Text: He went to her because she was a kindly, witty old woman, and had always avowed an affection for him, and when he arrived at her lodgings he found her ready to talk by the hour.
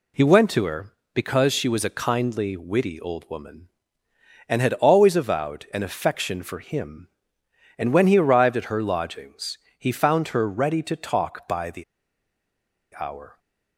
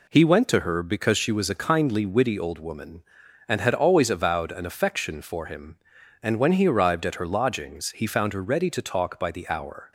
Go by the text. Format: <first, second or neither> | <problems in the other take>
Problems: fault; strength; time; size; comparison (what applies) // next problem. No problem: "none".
second | pauses between "lodgings" and "he"; slight; at 9.5 s; 0.20 s long // pauses between "the" and "hour"; at 11.8 s; 1.1 s long